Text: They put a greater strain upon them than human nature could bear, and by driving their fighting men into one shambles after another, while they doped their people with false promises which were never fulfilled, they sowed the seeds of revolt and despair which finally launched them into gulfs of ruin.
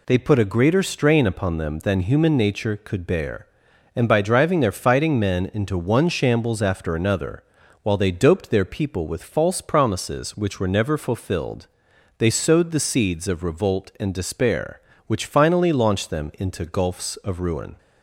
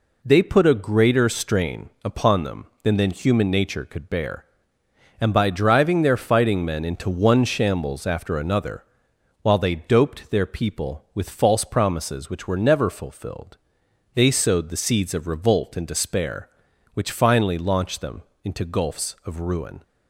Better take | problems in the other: first | pauses between "strain" and "upon"; slight; at 1.8 s; 0.16 s long // says "than" twice; at 2.9 s // pauses between "them" and "into"; slight; at 18.2 s; 0.22 s long

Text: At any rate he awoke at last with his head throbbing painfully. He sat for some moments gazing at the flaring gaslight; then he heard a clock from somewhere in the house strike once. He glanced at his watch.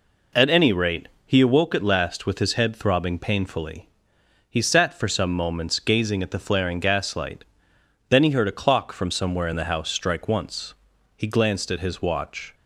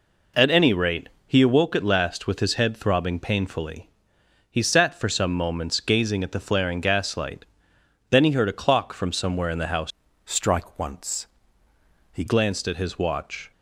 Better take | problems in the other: first | pauses between "rate" and "he"; slight; at 1.0 s; 0.18 s long; slight in the first // changes voice from "strike" to "He"; from 10.2 to 12.2 s; 2.0 s long

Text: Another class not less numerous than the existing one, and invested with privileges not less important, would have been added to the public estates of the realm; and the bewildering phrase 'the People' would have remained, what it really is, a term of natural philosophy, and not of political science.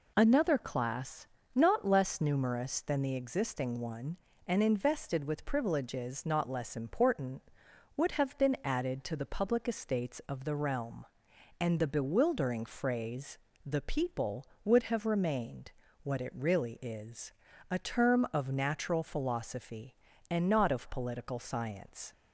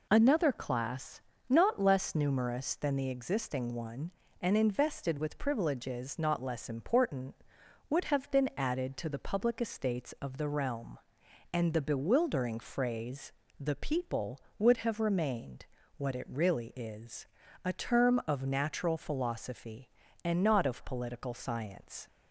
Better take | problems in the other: neither | pauses between "class" and "not"; slight; the same in both // pauses between "phrase" and "the"; slight; the same in both

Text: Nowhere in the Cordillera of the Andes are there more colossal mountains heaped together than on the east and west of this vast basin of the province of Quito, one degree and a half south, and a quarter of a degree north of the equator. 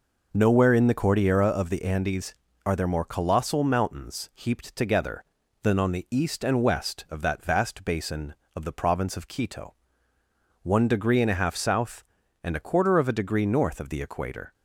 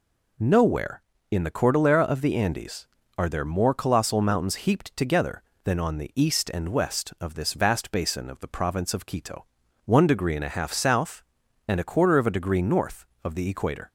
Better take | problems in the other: second | says "that" for "this"; at 7.2 s

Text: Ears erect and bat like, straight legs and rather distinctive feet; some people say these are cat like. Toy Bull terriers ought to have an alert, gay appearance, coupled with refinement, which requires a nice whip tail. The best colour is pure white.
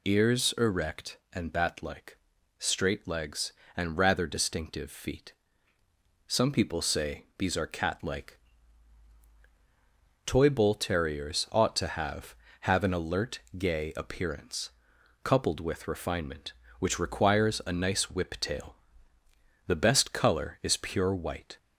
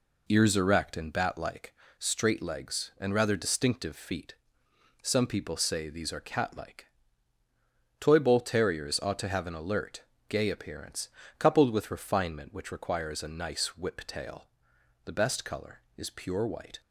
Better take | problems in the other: second | says "have" twice; at 12.6 s

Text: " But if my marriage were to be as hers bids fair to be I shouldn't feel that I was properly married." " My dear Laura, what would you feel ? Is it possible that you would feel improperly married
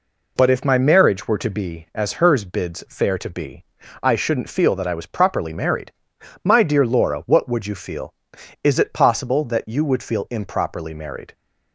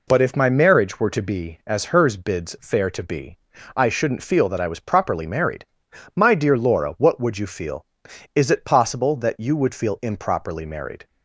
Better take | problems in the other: neither | pauses between "be" and "I"; the same in both

